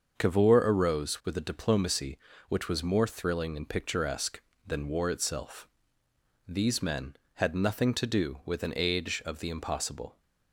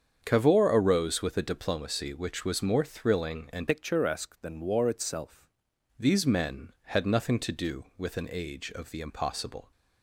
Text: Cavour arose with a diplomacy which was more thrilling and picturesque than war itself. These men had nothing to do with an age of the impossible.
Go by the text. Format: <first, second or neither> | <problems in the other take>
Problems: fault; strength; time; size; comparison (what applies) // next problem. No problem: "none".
first | starts louder than the rest; strong; until 1.2 s; 7.5 dB; also in the first // changes voice from "picturesque" to "itself"; from 3.6 to 5.4 s; 1.8 s long